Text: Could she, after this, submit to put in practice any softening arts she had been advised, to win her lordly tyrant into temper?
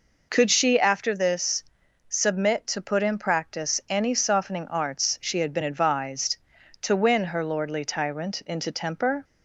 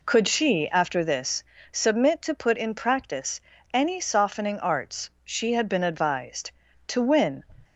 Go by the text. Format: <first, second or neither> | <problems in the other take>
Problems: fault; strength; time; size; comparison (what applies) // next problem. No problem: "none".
first | pauses between "practice" and "any"; slight; at 3.4 s; 0.32 s long // pauses between "arts" and "she"; slight; at 5.0 s; 0.16 s long // stops before "her lordly tyrant into temper"; at 7.6 s